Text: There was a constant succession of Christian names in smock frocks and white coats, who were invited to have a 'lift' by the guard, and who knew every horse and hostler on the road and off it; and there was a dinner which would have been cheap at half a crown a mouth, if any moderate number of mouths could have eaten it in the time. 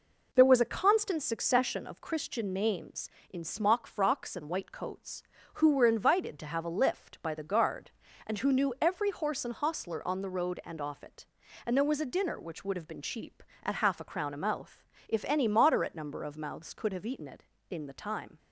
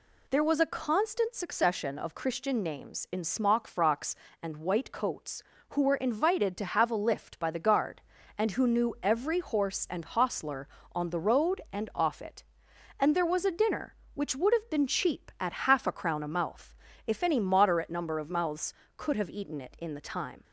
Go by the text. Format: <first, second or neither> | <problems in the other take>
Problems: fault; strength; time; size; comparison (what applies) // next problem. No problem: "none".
neither | none